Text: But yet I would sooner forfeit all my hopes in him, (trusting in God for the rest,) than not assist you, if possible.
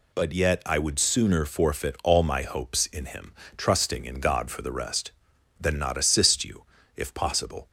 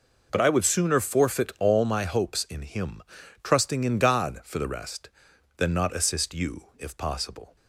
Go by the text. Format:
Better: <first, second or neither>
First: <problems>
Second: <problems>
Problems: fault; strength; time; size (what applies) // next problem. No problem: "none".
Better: first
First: none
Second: skips "yet"; at 0.4 s